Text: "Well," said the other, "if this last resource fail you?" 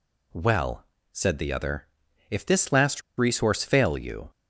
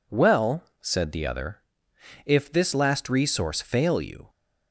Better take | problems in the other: second | pauses between "last" and "resource"; slight; at 3.0 s; 0.16 s long

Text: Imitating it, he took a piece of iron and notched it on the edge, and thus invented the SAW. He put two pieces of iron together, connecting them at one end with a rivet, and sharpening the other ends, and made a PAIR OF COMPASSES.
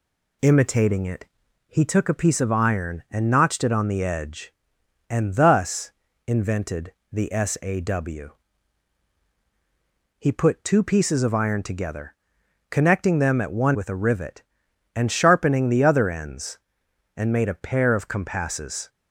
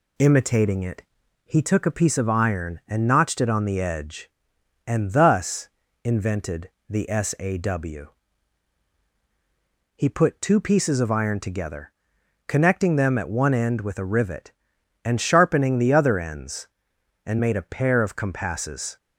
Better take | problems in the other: second | pauses between "thus" and "invented"; slight; at 5.9 s; 0.36 s long; slight in the second // pauses between "invented" and "the"; slight; at 6.9 s; 0.18 s long; slight in the second // skips "end"; at 13.7 s

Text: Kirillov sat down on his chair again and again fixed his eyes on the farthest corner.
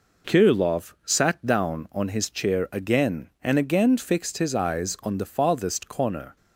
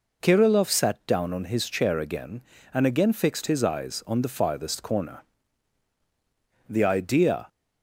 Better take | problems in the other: first | goes on to say "The idea"; noticeable; from 6.6 s on; 0.80 s long

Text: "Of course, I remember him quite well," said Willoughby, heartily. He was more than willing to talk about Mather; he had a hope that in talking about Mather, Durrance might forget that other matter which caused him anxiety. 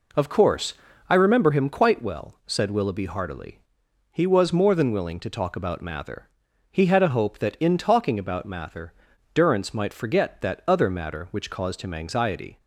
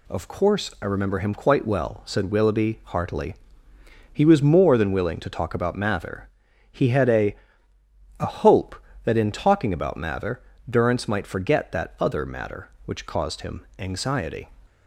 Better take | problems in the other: first | says "a" twice; at 8.2 s

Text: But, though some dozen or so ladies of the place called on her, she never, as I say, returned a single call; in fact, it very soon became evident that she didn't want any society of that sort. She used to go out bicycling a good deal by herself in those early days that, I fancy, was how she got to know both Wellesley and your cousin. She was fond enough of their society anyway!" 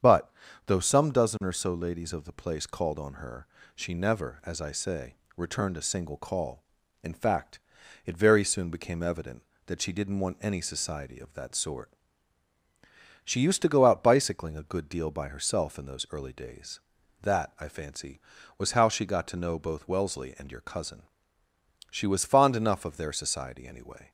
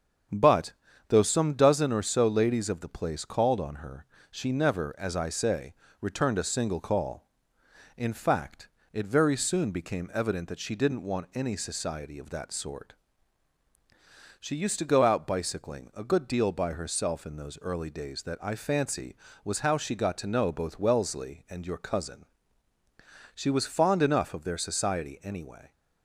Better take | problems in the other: neither | starts louder than the rest; strong; the same in both

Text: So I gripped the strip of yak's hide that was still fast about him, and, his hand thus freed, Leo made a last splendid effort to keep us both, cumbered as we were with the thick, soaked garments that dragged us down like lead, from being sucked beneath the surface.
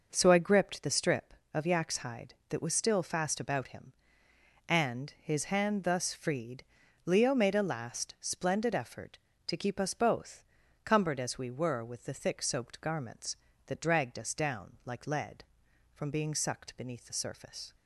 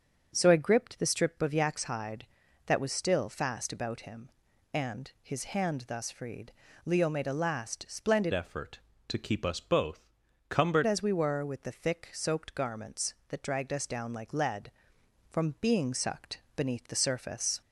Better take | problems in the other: first | starts louder than the rest; until 1.3 s; 6.5 dB // changes voice from "effort" to "cumbered"; from 8.3 to 10.8 s; 2.5 s long // pauses between "sucked" and "beneath"; slight; at 16.4 s; 0.16 s long

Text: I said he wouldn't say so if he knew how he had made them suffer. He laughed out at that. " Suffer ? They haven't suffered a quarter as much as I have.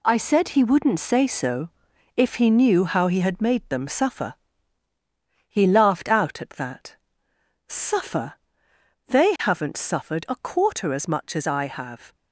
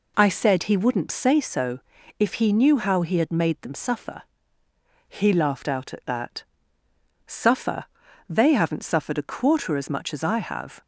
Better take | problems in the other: second | gets quieter; strong; throughout; 9.5 dB // pauses between "so" and "if"; noticeable; at 1.6 s; 0.46 s long; also in the second

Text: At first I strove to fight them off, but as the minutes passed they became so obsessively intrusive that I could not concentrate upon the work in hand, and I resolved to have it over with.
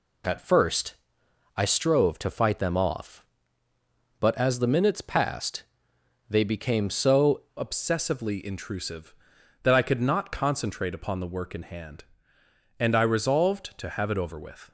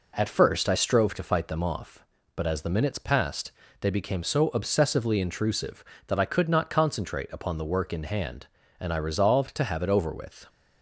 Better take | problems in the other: second | pauses between "first" and "I"; noticeable; at 0.9 s; 0.60 s long // pauses between "passed" and "they"; noticeable; at 5.6 s; 0.64 s long; slight in the second // changes voice at "obsessively"; from 7.5 s on; 7.2 s long

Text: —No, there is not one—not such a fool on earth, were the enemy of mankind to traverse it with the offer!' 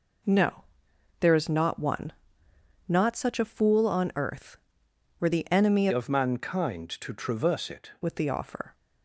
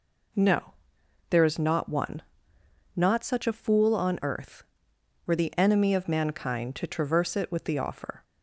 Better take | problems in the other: second | changes voice from "of" to "it"; from 5.9 to 7.9 s; 2.0 s long

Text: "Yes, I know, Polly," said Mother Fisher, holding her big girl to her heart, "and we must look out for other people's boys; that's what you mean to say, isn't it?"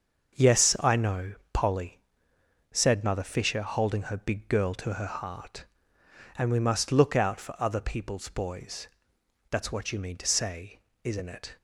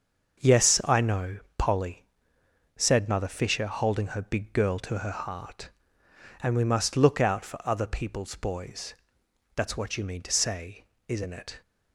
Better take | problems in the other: neither | starts louder than the rest; the same in both

